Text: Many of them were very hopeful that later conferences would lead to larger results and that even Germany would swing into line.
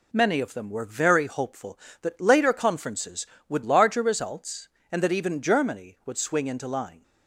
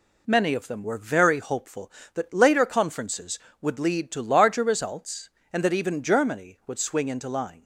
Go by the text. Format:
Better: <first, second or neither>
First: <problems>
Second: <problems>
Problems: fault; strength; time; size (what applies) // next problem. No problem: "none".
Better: second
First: skips "lead to"; at 3.6 s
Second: none